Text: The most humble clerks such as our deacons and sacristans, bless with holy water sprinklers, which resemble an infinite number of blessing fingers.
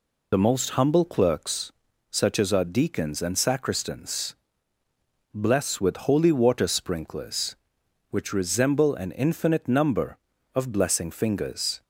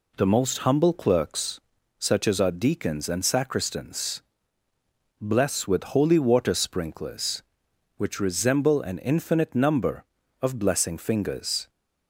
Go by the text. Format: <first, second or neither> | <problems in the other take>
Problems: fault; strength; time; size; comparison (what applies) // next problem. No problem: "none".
second | loses the start of "The"; at 0.3 s; 55 ms // pauses between "clerks" and "such"; at 1.7 s; 0.38 s long; also in the second